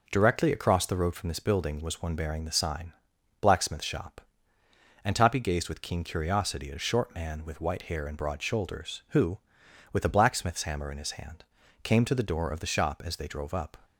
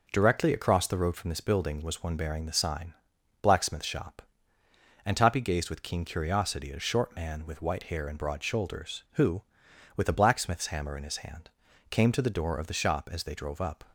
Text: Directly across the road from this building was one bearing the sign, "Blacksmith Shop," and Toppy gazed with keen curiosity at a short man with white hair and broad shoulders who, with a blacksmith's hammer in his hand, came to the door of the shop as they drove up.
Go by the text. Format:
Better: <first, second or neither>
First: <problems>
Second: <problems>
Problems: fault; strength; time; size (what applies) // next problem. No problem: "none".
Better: neither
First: none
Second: none